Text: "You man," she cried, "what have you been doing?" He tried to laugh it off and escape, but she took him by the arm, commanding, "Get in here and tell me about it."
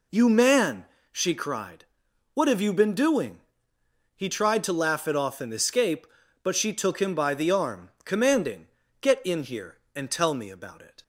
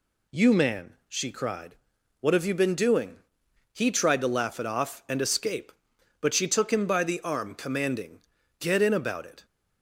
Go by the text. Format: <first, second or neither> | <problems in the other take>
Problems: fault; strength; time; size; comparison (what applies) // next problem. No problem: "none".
first | skips "here and tell me"; at 8.9 s